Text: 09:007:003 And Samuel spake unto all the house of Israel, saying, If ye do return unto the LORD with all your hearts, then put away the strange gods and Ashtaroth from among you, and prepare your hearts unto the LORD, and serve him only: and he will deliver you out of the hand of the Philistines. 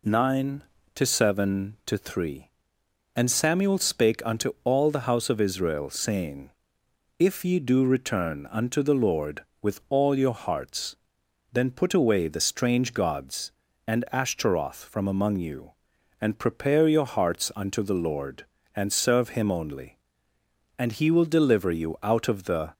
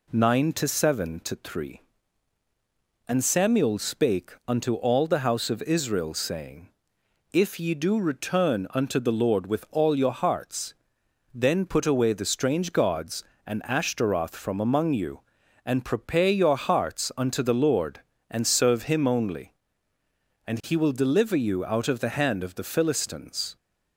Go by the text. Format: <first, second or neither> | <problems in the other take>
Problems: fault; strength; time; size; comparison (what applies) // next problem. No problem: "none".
second | stops before "hand of the Philistines"; at 22.7 s